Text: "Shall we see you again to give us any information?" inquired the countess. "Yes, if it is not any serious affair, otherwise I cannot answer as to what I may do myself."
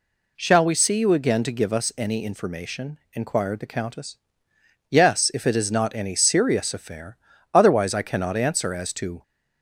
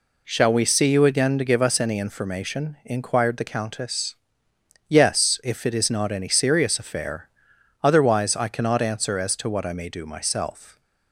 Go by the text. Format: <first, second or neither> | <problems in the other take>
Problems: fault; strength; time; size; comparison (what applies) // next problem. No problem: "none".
second | stops before "what I may do myself"; at 9.2 s